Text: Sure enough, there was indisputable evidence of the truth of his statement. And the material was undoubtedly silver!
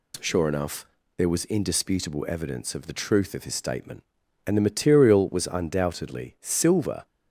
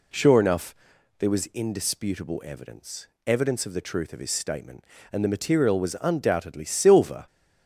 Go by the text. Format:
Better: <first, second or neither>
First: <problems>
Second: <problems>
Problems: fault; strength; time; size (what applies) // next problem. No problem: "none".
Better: first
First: none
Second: says "evidence" twice; at 3.2 s